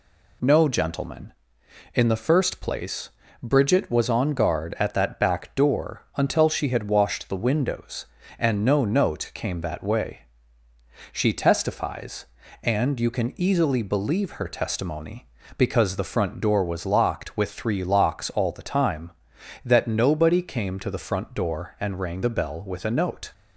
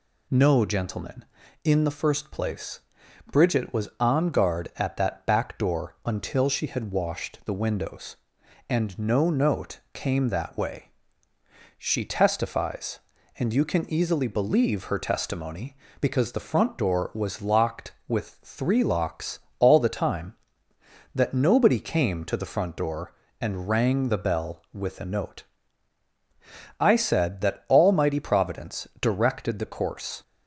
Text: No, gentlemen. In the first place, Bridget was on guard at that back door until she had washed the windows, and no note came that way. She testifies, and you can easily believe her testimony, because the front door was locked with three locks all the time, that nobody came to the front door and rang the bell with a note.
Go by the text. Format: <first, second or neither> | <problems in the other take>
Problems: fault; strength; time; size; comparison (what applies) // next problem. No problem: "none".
first | pauses between "locks" and "all"; slight; at 19.3 s; 0.20 s long // goes on to say "I said that Almighty providence directed the course"; strong; from 26.7 s on; 3.4 s long